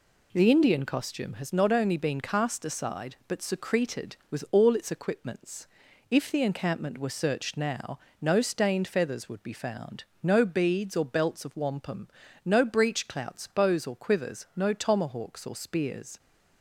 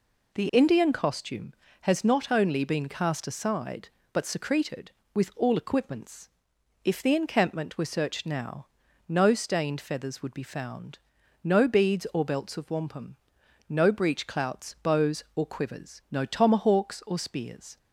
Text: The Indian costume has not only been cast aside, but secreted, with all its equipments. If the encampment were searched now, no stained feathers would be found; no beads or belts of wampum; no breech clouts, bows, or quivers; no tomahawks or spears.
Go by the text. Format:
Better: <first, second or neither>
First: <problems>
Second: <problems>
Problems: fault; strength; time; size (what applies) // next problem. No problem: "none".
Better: first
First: none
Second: skips "its"; at 5.5 s